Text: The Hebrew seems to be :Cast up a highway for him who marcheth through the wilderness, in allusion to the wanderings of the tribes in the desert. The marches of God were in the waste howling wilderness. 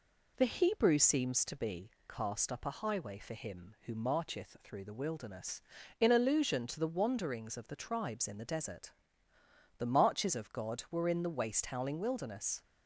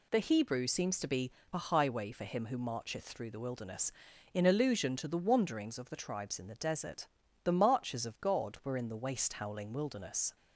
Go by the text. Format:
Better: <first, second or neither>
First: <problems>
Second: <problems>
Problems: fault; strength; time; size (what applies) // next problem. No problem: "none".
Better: first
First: none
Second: skips "Cast up"; at 1.4 s